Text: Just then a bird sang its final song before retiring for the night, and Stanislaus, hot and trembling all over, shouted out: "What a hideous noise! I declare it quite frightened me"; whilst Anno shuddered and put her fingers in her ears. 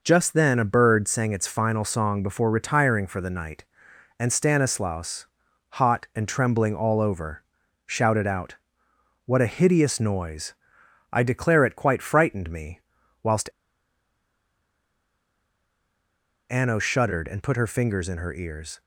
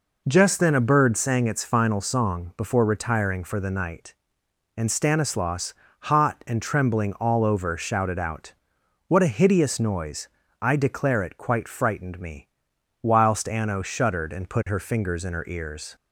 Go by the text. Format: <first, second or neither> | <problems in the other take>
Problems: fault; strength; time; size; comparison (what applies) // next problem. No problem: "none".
second | pauses between "whilst" and "Anno"; strong; at 13.4 s; 3.0 s long